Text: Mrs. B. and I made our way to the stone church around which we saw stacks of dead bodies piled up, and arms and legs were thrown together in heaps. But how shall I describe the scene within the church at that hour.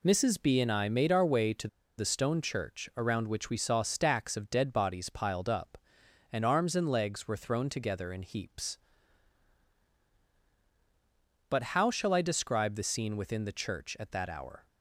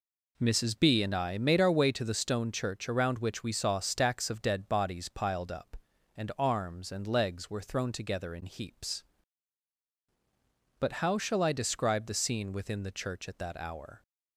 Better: second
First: pauses between "to" and "the"; slight; at 1.6 s; 0.30 s long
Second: none

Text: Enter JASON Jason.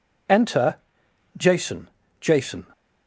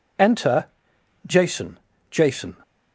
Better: neither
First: pauses between "Enter" and "JASON"; noticeable; at 0.7 s; 0.60 s long // pauses between "JASON" and "Jason"; slight; at 1.8 s; 0.31 s long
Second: pauses between "Enter" and "JASON"; noticeable; at 0.6 s; 0.59 s long // pauses between "JASON" and "Jason"; slight; at 1.7 s; 0.32 s long

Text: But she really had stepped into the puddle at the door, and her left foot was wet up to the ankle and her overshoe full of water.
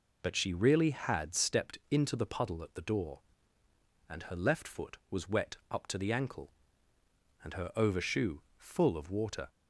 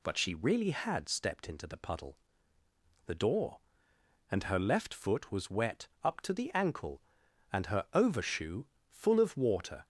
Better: first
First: pauses between "overshoe" and "full"; slight; at 8.4 s; 0.16 s long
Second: skips "at"; at 2.6 s // pauses between "wet" and "up"; slight; at 5.8 s; 0.16 s long // pauses between "overshoe" and "full"; slight; at 8.6 s; 0.24 s long

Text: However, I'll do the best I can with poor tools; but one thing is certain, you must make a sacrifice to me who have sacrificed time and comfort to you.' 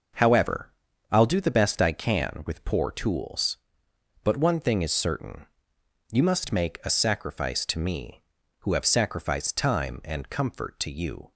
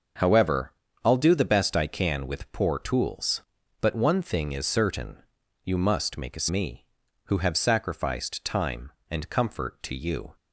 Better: first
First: none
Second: starts louder than the rest; until 1.5 s; 6 dB // skips "sacrifice to"; at 6.4 s

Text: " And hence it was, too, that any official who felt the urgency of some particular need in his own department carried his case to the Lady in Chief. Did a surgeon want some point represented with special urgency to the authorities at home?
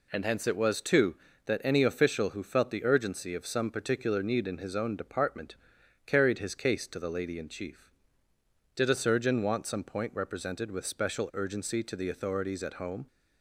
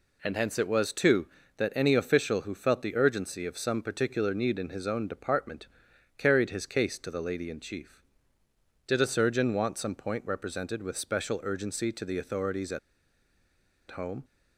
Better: first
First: pauses between "department" and "carried"; noticeable; at 5.5 s; 0.52 s long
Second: pauses between "department" and "carried"; noticeable; at 5.6 s; 0.52 s long // pauses between "at" and "home"; at 12.7 s; 1.1 s long

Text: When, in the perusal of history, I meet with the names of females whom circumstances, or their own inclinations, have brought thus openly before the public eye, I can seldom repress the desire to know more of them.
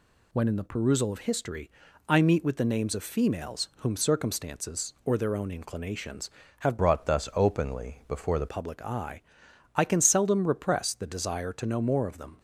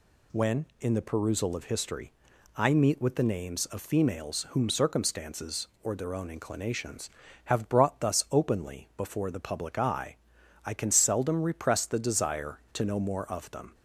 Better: second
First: changes voice from "brought" to "the"; from 6.7 to 8.4 s; 1.7 s long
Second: none

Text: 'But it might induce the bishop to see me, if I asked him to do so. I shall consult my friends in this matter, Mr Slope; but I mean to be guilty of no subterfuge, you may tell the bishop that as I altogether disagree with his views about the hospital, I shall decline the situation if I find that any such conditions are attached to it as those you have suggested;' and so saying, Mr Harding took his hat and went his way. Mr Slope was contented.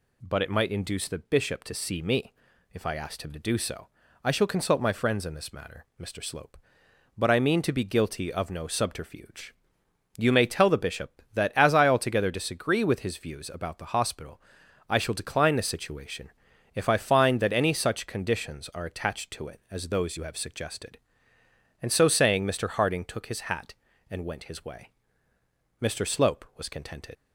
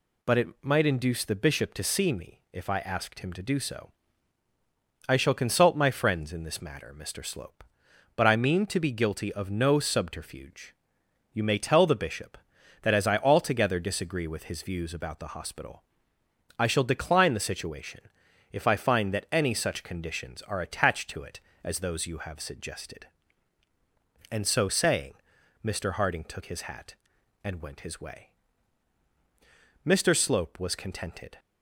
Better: second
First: pauses between "situation" and "if"; at 16.3 s; 0.44 s long // leaves "contented" unfinished; at 27.1 s; 80 ms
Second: pauses between "situation" and "if"; noticeable; at 18.0 s; 0.50 s long

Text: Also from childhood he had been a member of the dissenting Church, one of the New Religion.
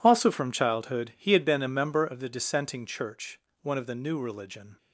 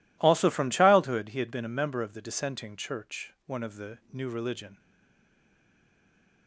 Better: first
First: none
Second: stays silent after the last word; noticeable; from 4.7 s on; 1.7 s long

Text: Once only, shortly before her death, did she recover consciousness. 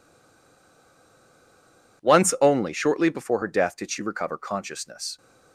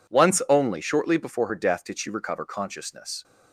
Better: second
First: stays silent before the first word; noticeable; until 2.0 s; 2.0 s long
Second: none

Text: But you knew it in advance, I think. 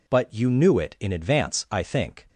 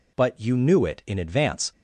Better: first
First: none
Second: stops before "I think"; at 1.7 s

